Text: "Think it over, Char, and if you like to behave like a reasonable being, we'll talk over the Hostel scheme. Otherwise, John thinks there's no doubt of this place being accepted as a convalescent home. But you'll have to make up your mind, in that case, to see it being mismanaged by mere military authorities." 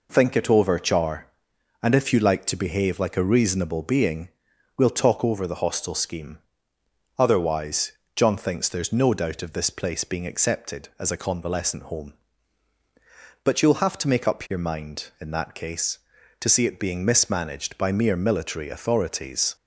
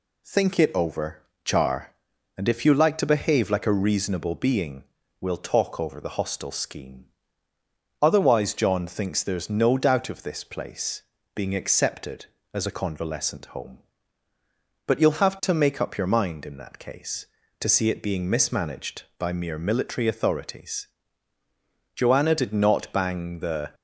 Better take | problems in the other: first | pauses between "place" and "being"; slight; at 11.0 s; 0.32 s long // goes on to say "Joanna did not bang the"; strong; from 21.9 s on; 1.8 s long

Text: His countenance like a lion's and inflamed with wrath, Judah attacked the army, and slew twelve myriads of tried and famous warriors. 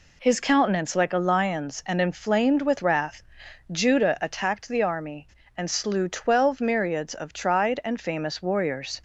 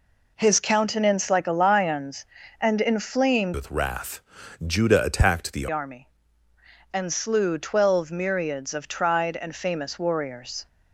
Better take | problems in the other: first | changes voice from "with" to "the"; from 3.5 to 5.6 s; 2.1 s long

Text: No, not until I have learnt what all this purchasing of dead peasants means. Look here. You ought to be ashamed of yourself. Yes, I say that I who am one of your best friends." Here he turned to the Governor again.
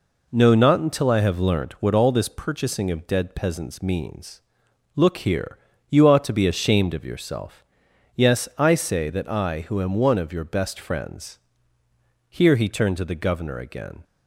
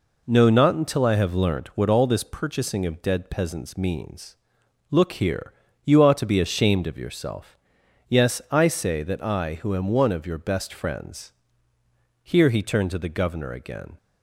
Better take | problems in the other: neither | none

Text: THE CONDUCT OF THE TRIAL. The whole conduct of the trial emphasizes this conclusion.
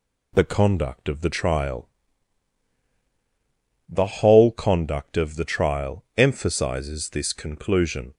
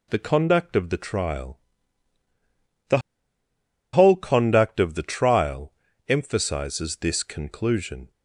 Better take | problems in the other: first | pauses between "The" and "whole"; noticeable; at 2.9 s; 0.95 s long // pauses between "trial" and "emphasizes"; slight; at 5.7 s; 0.36 s long

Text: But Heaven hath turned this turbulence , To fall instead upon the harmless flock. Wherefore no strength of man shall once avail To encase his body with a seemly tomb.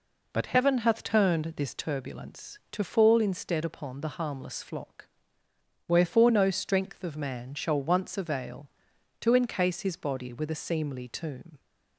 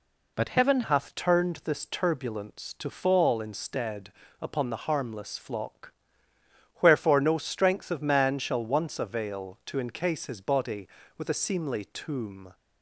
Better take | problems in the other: first | changes voice at "hath"; from 0.8 s on; 11.7 s long // pauses between "instead" and "upon"; slight; at 4.1 s; 0.28 s long

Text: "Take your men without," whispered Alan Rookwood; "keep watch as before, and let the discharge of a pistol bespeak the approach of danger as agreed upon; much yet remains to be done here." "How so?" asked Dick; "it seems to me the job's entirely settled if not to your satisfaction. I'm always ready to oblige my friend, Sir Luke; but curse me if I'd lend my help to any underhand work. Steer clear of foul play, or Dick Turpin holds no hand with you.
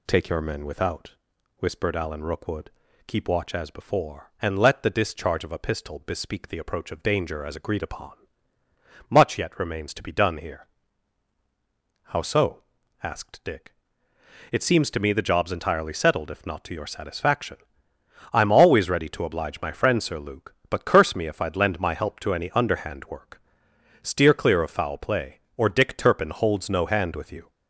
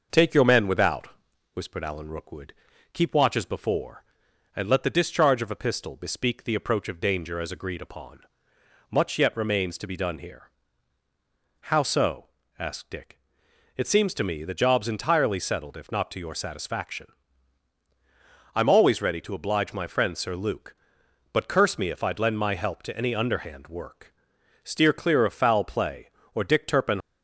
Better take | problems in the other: first | stops before "holds no hand with you"; at 27.0 s

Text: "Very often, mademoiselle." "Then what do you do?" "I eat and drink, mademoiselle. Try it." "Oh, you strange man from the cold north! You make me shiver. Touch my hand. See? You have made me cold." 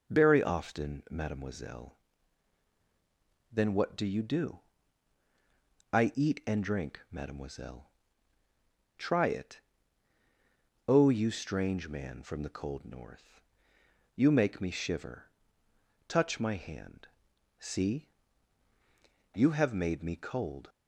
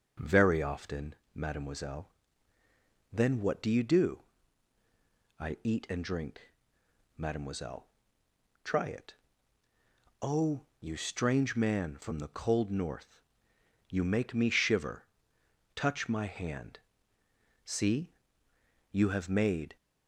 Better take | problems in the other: first | starts louder than the rest; until 1.3 s; 6.5 dB; noticeable in the first // stops before "me cold"; at 19.7 s

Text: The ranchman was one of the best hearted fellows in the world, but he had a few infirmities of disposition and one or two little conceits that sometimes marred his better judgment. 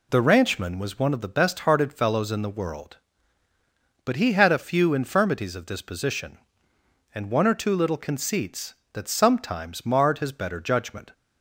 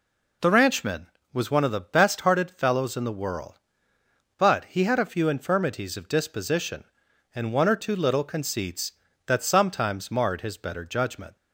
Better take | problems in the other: neither | none

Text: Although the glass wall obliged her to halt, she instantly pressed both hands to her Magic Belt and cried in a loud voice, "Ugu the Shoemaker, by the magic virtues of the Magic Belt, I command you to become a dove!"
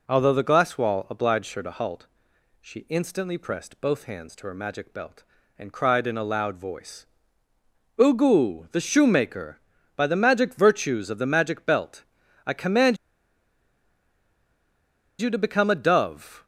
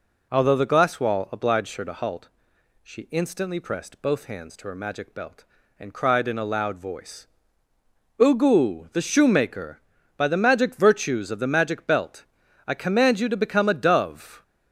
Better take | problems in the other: second | pauses between "command" and "you"; strong; at 12.9 s; 2.2 s long

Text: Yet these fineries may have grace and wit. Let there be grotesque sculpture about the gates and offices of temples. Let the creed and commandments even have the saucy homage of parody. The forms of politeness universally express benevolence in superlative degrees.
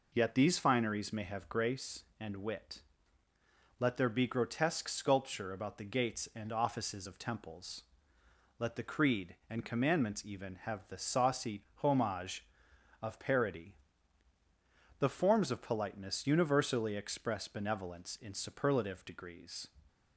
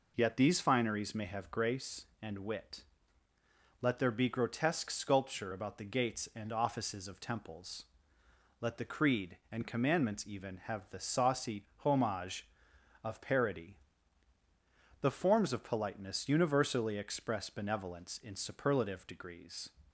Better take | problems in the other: neither | pauses between "saucy" and "homage"; slight; the same in both

